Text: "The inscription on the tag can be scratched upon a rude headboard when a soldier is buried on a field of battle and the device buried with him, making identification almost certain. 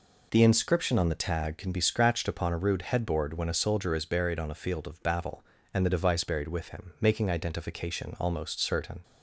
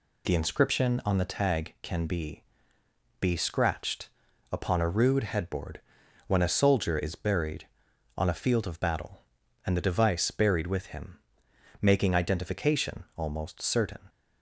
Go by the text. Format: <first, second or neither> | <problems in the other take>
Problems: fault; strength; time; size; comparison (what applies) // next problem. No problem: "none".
first | says "be" twice; at 3.2 s // pauses between "scratched" and "upon"; at 4.0 s; 0.42 s long // pauses between "headboard" and "when"; noticeable; at 5.8 s; 0.46 s long